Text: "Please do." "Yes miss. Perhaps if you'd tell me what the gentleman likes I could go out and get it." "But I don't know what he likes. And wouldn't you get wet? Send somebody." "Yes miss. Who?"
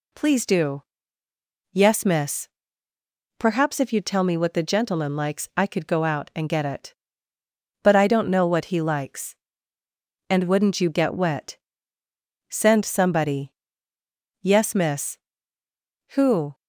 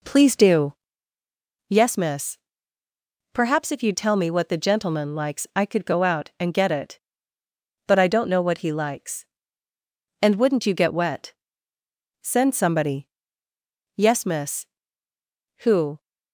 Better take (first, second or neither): first